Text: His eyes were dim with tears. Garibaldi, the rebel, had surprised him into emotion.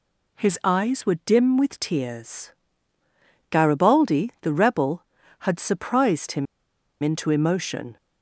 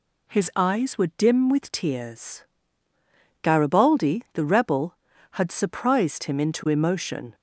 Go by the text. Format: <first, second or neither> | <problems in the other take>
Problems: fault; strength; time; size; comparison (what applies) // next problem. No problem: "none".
second | pauses between "him" and "into"; noticeable; at 6.4 s; 0.56 s long